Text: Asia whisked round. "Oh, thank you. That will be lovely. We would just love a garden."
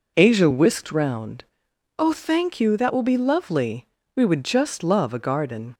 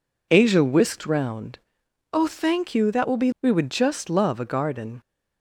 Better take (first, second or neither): first